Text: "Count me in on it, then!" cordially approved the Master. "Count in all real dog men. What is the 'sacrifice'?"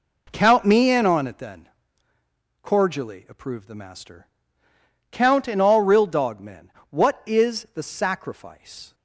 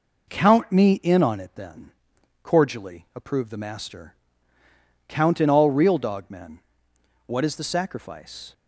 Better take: neither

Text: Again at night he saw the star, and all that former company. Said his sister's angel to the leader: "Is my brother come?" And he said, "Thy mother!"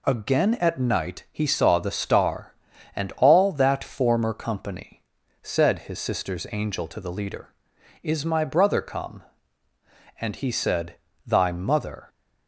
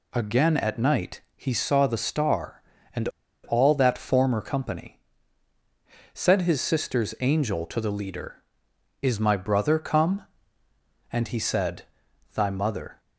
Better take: first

